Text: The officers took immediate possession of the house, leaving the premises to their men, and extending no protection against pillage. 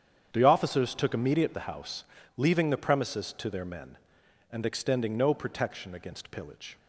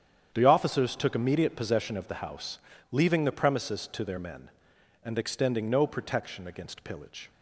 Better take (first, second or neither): second